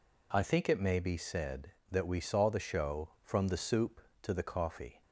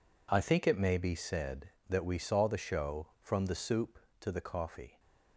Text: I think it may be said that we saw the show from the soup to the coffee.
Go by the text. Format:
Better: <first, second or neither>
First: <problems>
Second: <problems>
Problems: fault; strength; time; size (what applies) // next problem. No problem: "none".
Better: first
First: none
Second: gets quieter; strong; throughout; 13 dB